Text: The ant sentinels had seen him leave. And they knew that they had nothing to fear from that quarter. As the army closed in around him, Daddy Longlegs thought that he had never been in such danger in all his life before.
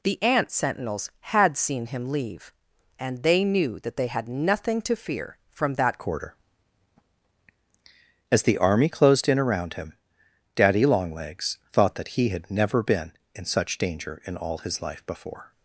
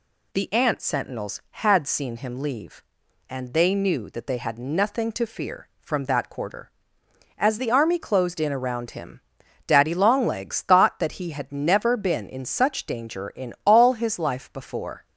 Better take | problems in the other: second | changes voice at "quarter"; from 5.9 s on; 9.6 s long

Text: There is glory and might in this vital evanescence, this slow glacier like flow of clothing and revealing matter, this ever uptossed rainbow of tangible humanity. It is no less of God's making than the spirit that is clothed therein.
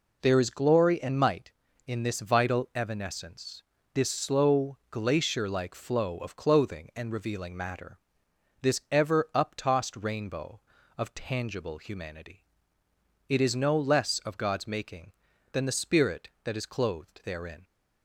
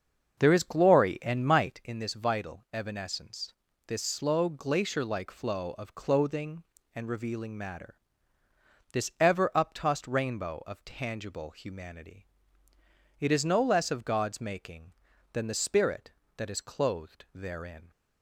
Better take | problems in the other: first | starts louder than the rest; until 2.0 s; 6.5 dB

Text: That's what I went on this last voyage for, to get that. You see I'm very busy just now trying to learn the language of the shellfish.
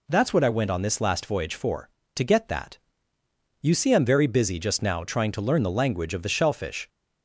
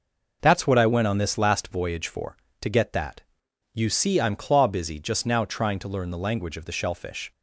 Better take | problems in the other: first | says "claw" for "very"; at 4.3 s

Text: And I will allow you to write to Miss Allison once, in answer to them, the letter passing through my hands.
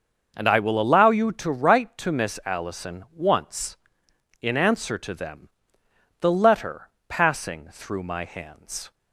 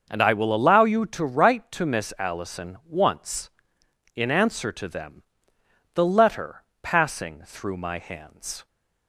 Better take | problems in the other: neither | starts louder than the rest; the same in both // pauses between "letter" and "passing"; slight; the same in both

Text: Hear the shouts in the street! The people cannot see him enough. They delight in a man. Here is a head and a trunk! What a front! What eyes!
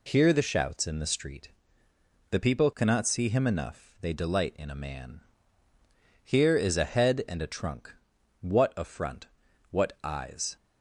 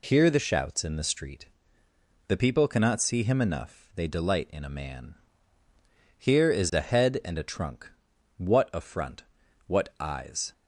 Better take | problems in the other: neither | none

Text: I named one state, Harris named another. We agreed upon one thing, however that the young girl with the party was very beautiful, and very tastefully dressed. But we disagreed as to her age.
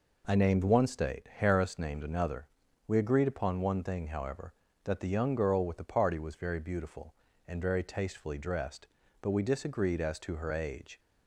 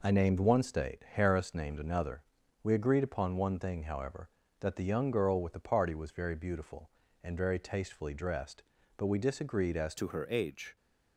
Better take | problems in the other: first | changes voice at "to"; from 9.9 s on; 0.8 s long

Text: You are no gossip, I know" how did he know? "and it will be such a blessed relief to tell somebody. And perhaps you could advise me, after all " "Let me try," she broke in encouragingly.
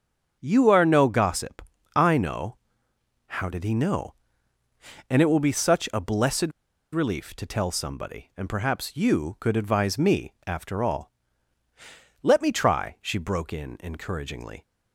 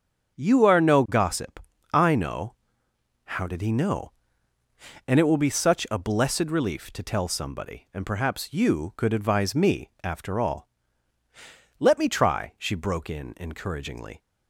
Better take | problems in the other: second | starts louder than the rest; strong; until 1.4 s; 7 dB; strong in the second // pauses between "know" and "how"; noticeable; at 2.5 s; 0.68 s long; noticeable in the second // pauses between "blessed" and "relief"; at 6.5 s; 0.41 s long

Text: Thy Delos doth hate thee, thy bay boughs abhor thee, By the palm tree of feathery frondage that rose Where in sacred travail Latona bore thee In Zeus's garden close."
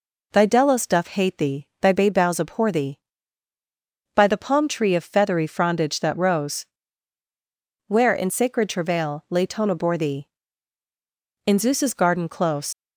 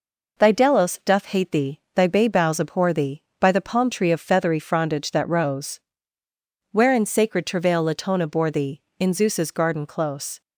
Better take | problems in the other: second | pauses between "rose" and "Where"; at 6.6 s; 1.2 s long; noticeable in the second // leaves "close" unfinished; at 12.7 s; 80 ms

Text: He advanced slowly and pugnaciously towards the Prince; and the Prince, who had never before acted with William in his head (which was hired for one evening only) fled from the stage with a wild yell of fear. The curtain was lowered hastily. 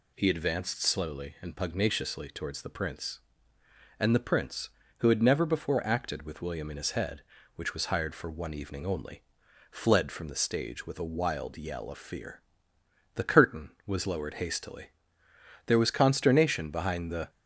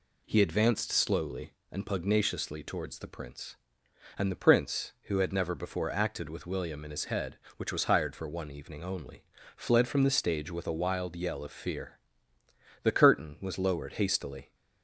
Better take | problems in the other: second | goes on to say "There was consternation behind the"; from 15.6 s on; 1.6 s long

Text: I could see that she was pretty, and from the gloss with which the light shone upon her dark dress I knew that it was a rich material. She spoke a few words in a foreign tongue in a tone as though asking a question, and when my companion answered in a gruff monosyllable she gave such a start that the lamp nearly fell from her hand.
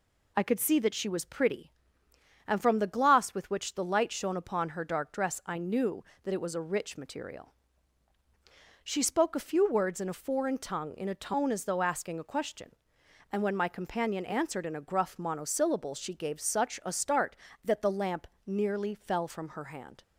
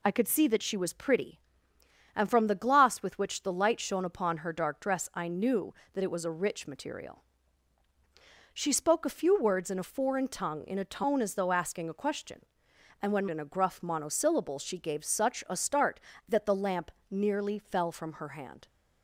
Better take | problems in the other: first | skips "my companion answered"; at 13.2 s // pauses between "lamp" and "nearly"; slight; at 16.8 s; 0.20 s long; slight in the first

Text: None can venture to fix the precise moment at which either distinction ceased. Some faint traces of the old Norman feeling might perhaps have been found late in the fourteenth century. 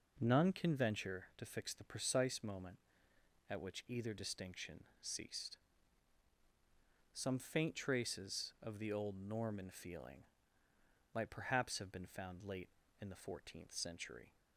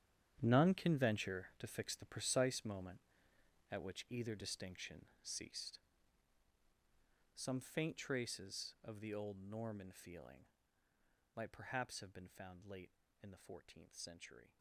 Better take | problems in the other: first | gets quieter; strong; throughout; 15.5 dB // pauses between "distinction" and "ceased"; slight; at 5.0 s; 0.18 s long; slight in the first // pauses between "feeling" and "might"; noticeable; at 10.4 s; 0.90 s long; noticeable in the first

